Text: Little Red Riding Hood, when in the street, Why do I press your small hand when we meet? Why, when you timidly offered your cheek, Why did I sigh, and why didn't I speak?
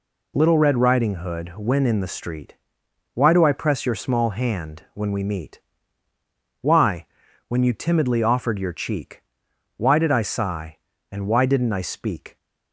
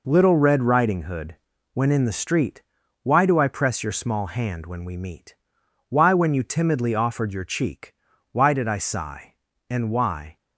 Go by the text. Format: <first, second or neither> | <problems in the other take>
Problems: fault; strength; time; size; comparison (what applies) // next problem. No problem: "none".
first | stops before "didn't I speak"; at 10.3 s